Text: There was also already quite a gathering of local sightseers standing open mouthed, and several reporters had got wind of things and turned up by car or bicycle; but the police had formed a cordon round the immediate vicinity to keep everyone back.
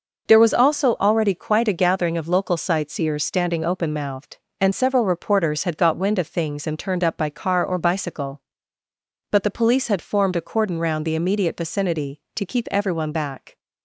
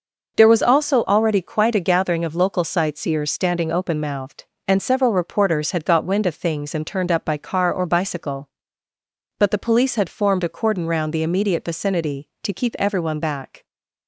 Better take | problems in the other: neither | none

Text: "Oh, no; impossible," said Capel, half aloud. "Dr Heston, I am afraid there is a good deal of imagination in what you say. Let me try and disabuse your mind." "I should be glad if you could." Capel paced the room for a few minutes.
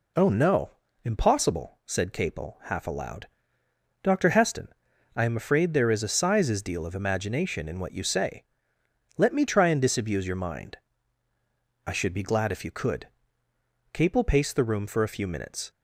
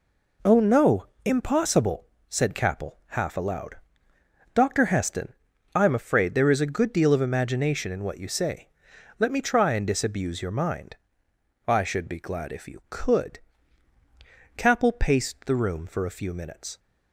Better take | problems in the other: second | says "sizes" for "good"; at 6.0 s

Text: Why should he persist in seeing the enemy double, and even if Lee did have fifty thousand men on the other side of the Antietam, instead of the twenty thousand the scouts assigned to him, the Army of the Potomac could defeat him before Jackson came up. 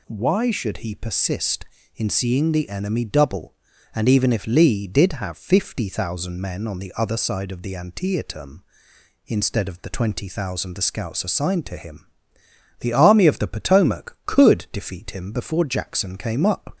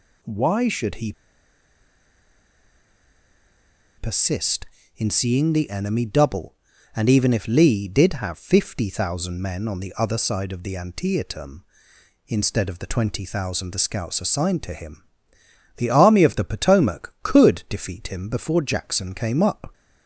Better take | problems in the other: first | pauses between "he" and "persist"; strong; at 1.1 s; 2.8 s long

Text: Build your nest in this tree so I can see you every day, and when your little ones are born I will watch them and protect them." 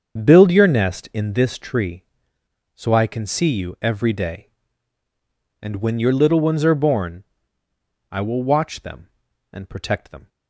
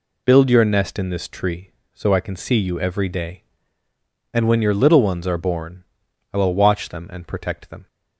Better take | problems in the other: second | starts louder than the rest; until 1.4 s; 7 dB // pauses between "born" and "I"; noticeable; at 7.2 s; 0.88 s long; noticeable in the second

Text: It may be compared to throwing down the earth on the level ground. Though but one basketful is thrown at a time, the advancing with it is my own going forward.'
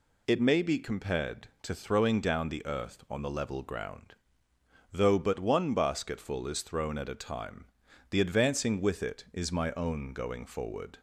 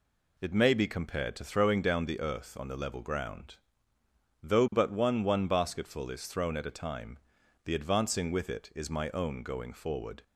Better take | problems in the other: first | says "one" twice; at 5.2 s

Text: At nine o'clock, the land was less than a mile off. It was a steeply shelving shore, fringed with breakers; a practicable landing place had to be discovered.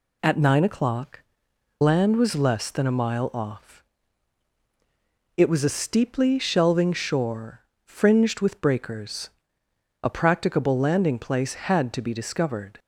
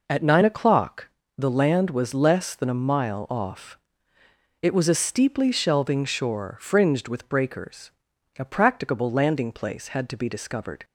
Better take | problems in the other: second | skips "the"; at 1.5 s

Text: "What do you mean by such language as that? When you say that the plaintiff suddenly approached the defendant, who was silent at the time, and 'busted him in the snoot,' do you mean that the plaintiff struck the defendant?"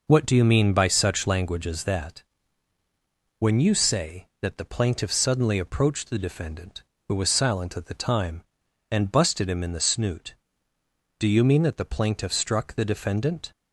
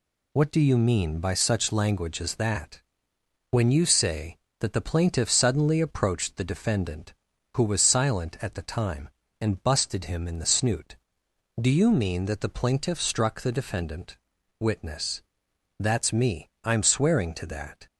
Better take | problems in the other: first | goes on to say "WITNESS That's me I'm swearing to that"; strong; from 14.6 s on; 3.2 s long

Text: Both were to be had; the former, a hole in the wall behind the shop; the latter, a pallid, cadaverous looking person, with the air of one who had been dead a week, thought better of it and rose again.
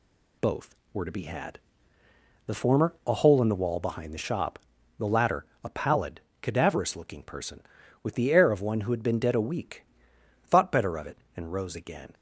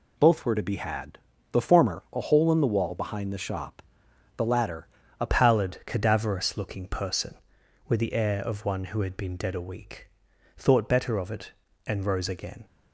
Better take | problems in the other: first | changes voice at "pallid"; from 5.2 s on; 7.4 s long

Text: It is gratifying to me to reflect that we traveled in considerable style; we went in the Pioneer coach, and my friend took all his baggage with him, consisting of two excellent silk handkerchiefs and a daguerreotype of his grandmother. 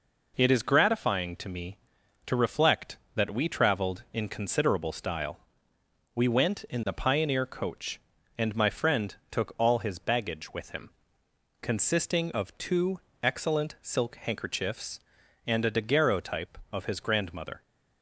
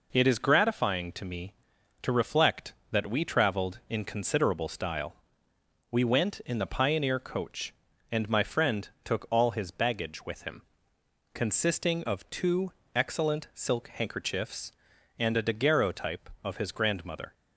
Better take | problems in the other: neither | pauses between "friend" and "took"; slight; the same in both // pauses between "two" and "excellent"; slight; the same in both

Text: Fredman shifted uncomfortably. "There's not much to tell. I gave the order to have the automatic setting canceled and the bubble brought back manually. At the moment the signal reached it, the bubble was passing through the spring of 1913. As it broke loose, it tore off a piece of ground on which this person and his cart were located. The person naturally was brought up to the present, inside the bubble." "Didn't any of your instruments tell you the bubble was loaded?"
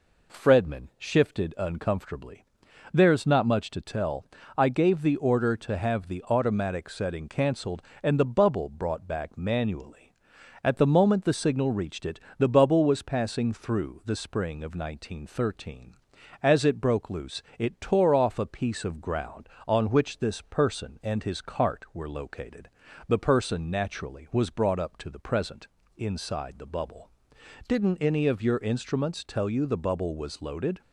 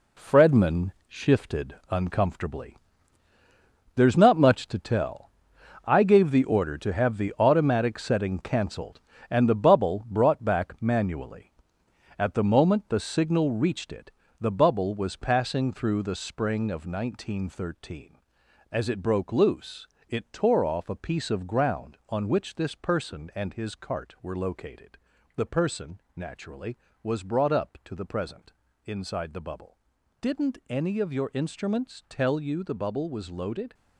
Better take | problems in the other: first | gets quieter; strong; throughout; 8.5 dB // pauses between "Fredman" and "shifted"; slight; at 0.9 s; 0.16 s long // pauses between "person" and "naturally"; slight; at 25.9 s; 0.16 s long

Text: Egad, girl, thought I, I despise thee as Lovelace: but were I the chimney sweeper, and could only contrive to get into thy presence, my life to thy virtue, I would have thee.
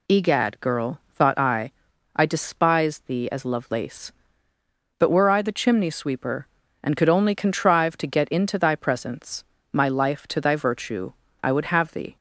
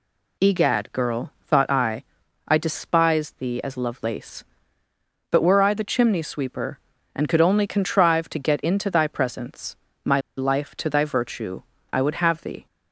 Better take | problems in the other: first | pauses between "my" and "life"; slight; at 10.1 s; 0.17 s long

